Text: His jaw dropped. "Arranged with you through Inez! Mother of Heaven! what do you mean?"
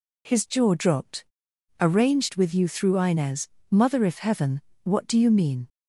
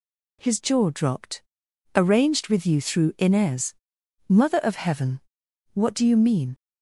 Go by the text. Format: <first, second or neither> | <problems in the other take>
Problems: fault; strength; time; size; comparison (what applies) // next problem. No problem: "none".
second | says "if" for "of"; at 4.0 s